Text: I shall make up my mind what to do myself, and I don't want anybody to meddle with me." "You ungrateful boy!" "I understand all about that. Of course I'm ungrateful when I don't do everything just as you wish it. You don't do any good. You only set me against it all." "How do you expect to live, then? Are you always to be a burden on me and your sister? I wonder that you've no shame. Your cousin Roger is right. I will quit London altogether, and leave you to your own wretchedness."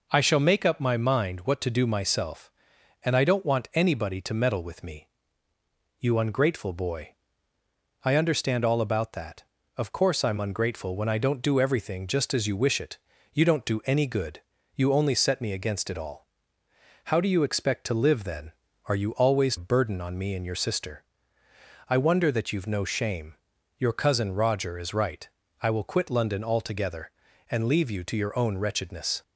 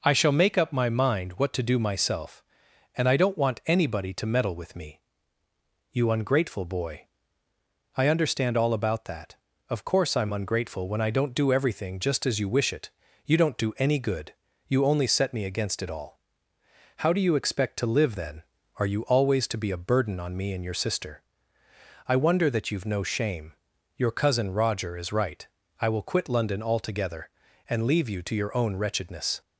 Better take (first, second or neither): second